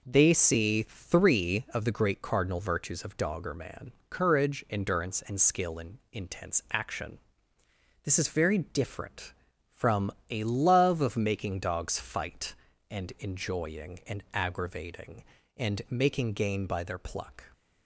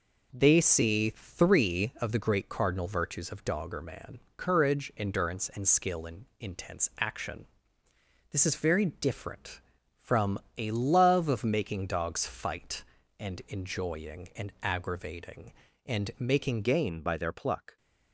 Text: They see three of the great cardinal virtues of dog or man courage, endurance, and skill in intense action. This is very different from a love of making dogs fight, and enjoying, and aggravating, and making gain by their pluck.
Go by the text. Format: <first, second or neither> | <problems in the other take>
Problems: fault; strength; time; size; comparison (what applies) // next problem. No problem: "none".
first | pauses between "man" and "courage"; slight; at 4.1 s; 0.18 s long; slight in the first // pauses between "from" and "a"; slight; at 10.3 s; 0.18 s long; slight in the first // changes voice at "gain"; from 16.6 s on; 1.1 s long